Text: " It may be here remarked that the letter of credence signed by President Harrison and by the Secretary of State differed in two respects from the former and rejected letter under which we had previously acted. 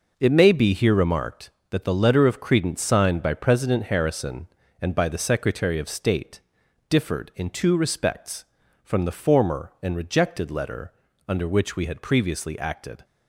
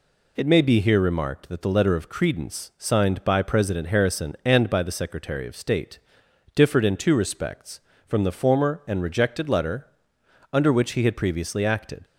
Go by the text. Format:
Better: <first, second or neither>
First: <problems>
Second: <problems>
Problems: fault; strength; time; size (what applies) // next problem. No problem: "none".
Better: first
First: pauses between "State" and "differed"; noticeable; at 6.3 s; 0.48 s long // pauses between "letter" and "under"; slight; at 10.9 s; 0.34 s long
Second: pauses between "State" and "differed"; noticeable; at 5.9 s; 0.56 s long // pauses between "letter" and "under"; noticeable; at 9.8 s; 0.66 s long // says "he" for "we"; at 10.9 s